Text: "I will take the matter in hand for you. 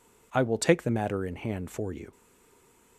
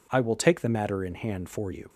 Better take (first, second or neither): second